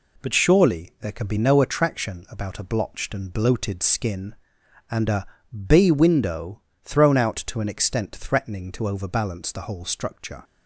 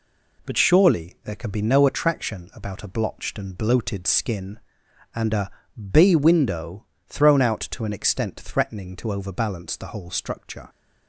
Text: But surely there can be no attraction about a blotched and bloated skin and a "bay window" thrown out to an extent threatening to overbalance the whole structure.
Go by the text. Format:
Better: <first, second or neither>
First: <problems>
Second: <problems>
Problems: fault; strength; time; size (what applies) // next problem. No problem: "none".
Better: neither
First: pauses between "a" and "bay"; at 5.2 s; 0.40 s long // pauses between "window" and "thrown"; slight; at 6.6 s; 0.22 s long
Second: pauses between "a" and "bay"; at 5.5 s; 0.40 s long // pauses between "window" and "thrown"; slight; at 6.8 s; 0.22 s long